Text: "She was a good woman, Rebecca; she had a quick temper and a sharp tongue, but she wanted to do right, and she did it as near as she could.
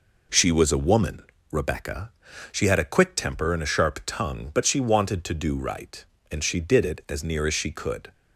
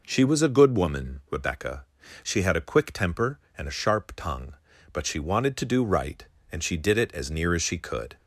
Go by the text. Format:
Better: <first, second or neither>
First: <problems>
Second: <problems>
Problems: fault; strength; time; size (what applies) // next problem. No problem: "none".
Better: second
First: skips "good"; at 0.7 s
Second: none